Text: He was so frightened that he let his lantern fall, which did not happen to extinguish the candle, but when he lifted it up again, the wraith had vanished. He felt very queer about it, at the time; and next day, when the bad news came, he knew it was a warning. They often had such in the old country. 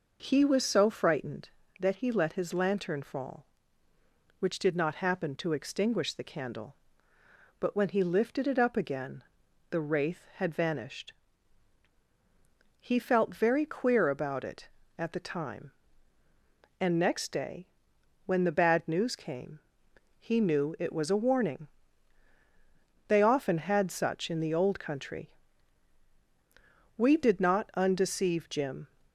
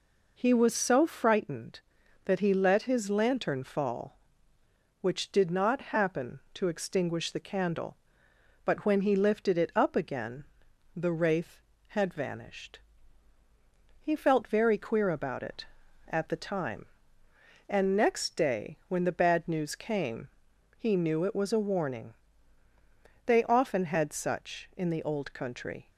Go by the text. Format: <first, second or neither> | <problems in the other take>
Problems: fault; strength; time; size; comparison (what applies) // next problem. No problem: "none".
second | goes on to say "We did not undeceive Jim"; strong; from 26.9 s on; 1.9 s long